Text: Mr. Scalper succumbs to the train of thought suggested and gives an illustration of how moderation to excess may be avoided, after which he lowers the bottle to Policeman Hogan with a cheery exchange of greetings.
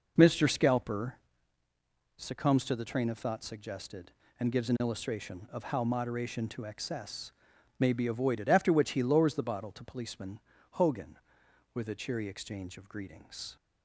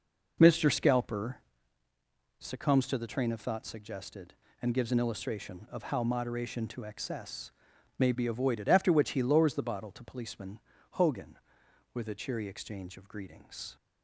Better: neither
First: pauses between "Scalper" and "succumbs"; at 1.1 s; 1.0 s long // pauses between "excess" and "may"; noticeable; at 7.3 s; 0.48 s long // pauses between "Policeman" and "Hogan"; slight; at 10.3 s; 0.32 s long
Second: pauses between "Scalper" and "succumbs"; at 1.3 s; 1.0 s long // pauses between "excess" and "may"; noticeable; at 7.5 s; 0.48 s long // pauses between "Policeman" and "Hogan"; slight; at 10.5 s; 0.32 s long

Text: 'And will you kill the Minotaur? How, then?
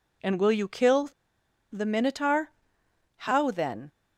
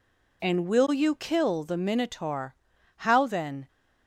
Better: second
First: pauses between "kill" and "the"; noticeable; at 1.0 s; 0.62 s long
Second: none

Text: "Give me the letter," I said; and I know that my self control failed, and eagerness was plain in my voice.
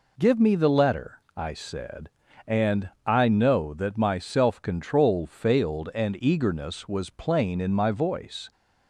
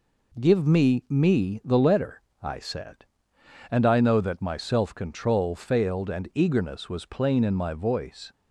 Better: first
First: none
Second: says "me" twice; at 1.1 s

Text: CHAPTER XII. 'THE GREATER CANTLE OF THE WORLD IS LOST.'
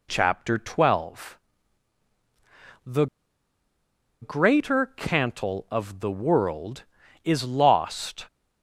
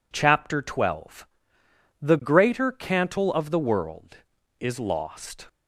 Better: second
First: pauses between "THE" and "GREATER"; at 3.0 s; 1.1 s long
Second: none

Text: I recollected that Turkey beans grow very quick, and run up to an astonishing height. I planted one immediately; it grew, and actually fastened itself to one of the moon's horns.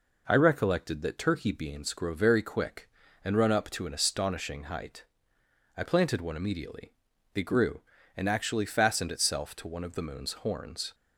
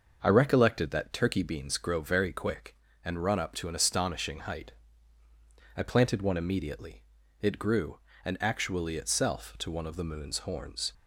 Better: first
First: none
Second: skips "fastened"; at 8.9 s

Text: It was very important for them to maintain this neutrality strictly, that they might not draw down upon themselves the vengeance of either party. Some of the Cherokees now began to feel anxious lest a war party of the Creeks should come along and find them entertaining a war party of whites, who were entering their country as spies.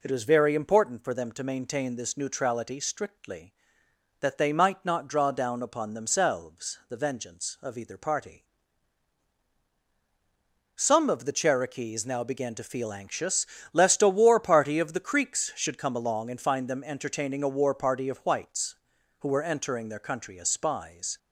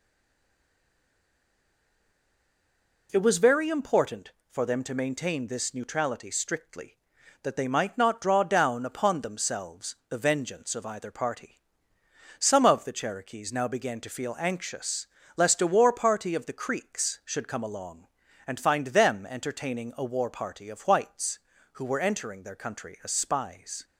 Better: first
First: pauses between "anxious" and "lest"; slight; at 13.4 s; 0.26 s long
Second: stays silent before the first word; strong; until 3.0 s; 3.0 s long // pauses between "anxious" and "lest"; slight; at 15.0 s; 0.30 s long

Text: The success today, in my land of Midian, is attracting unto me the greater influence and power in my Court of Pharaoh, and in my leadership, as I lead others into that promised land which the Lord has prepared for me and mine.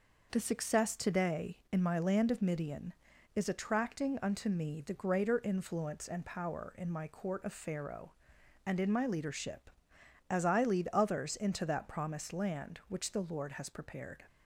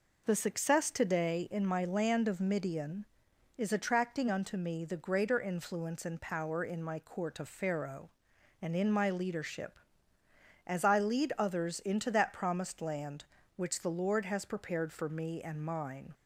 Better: second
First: stops before "for me and mine"; at 14.2 s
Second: none

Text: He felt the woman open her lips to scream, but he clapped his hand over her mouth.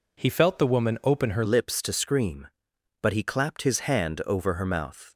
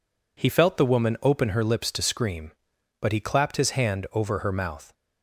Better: second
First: changes voice at "lips"; from 1.4 s on; 3.7 s long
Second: none

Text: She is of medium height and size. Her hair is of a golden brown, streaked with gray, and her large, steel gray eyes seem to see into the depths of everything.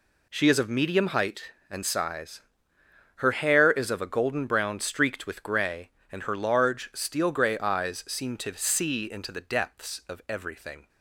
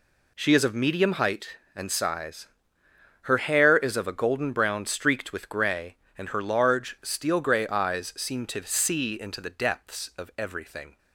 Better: neither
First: none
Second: none

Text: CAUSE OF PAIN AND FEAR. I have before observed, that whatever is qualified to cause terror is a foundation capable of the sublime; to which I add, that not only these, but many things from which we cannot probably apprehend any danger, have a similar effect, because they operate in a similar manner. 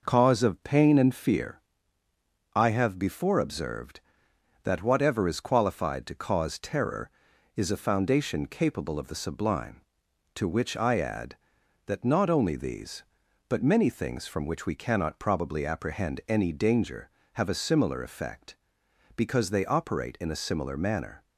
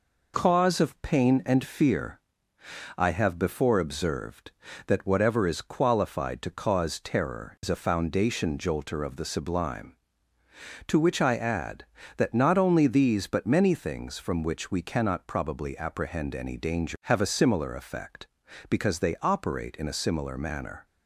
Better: first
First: none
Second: says "jolter" for "capable"; at 8.5 s

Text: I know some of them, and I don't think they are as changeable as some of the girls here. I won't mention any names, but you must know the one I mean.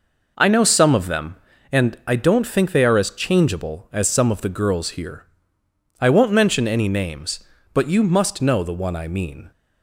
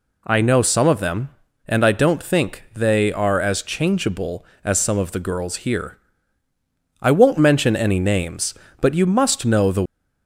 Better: first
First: none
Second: stops before "one I mean"; at 9.8 s

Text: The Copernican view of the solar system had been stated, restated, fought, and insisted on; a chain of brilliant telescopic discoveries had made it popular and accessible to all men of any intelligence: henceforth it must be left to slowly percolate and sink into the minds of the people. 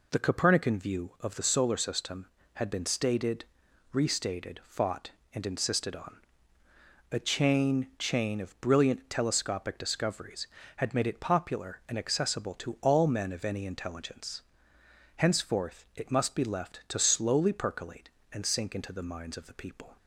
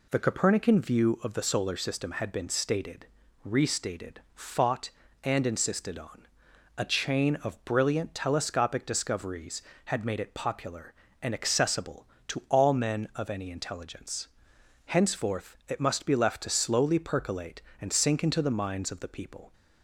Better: second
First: says "chain" twice; at 7.9 s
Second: none

